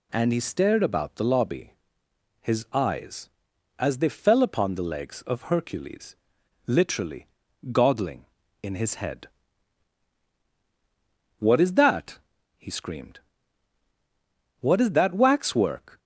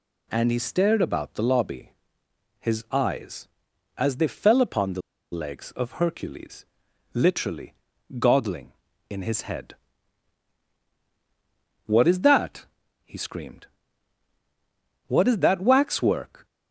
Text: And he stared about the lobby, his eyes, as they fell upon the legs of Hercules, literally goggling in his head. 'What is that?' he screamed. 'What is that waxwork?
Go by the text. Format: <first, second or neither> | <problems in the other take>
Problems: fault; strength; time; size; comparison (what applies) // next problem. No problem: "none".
first | pauses between "the" and "legs"; slight; at 4.9 s; 0.32 s long // pauses between "literally" and "goggling"; at 7.7 s; 0.44 s long; also in the first